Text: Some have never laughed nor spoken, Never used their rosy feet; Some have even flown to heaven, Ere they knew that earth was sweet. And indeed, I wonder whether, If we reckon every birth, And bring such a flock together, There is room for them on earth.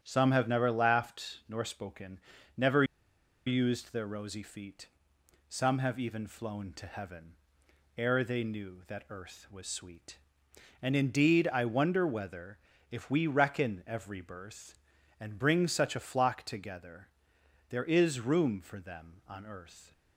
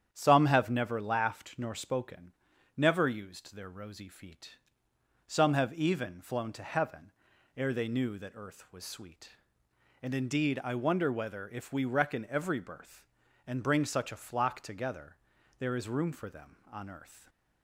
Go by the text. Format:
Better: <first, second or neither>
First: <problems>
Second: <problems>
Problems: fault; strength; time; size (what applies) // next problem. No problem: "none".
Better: second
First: starts louder than the rest; strong; until 1.0 s; 9 dB // pauses between "Never" and "used"; noticeable; at 2.8 s; 0.62 s long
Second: starts louder than the rest; strong; until 1.1 s; 9 dB